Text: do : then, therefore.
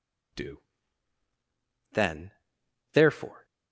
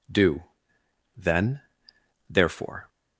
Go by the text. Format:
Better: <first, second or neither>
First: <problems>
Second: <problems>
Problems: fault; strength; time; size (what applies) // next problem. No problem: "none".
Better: neither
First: none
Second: none